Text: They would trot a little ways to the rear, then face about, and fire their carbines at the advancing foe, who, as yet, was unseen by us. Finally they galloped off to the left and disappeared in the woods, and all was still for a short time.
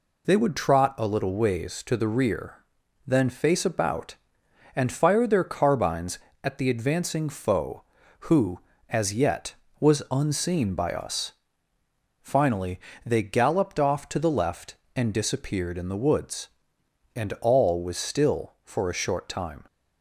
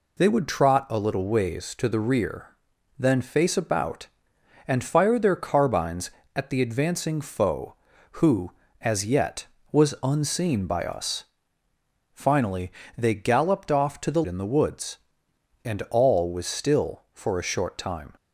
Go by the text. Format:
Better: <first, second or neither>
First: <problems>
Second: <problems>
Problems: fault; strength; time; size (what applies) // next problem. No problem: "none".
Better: first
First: pauses between "Finally" and "they"; slight; at 12.7 s; 0.24 s long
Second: pauses between "Finally" and "they"; slight; at 12.7 s; 0.24 s long // skips "left and disappeared"; at 14.2 s